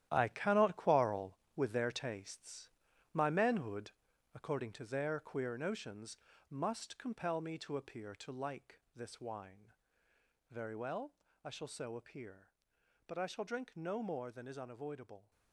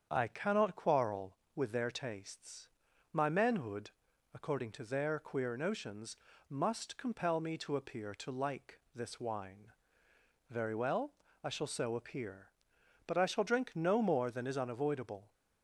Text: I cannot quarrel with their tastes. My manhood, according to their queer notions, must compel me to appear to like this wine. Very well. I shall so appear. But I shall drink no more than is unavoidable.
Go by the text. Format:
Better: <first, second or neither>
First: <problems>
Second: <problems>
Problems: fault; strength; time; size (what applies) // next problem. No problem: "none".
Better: second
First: gets quieter; strong; throughout; 10 dB // starts louder than the rest; strong; until 1.1 s; 12 dB // pauses between "like" and "this"; slight; at 8.8 s; 0.16 s long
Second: starts louder than the rest; strong; until 1.1 s; 7.5 dB // pauses between "like" and "this"; slight; at 8.7 s; 0.16 s long